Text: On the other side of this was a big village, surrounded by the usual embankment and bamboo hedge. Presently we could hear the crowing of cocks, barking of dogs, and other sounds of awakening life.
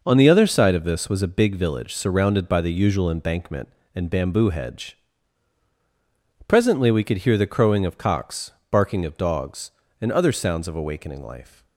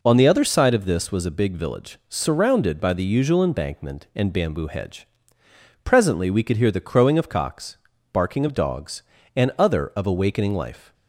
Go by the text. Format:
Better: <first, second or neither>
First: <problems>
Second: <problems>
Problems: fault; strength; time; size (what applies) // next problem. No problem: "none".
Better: first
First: none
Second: skips "sounds"; at 9.9 s